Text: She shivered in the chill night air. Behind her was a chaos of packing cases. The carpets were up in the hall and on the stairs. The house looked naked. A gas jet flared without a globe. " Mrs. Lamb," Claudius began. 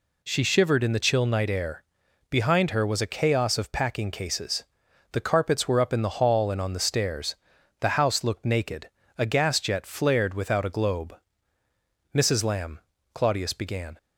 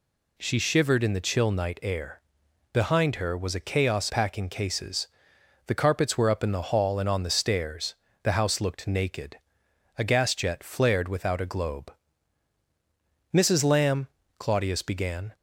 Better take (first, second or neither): first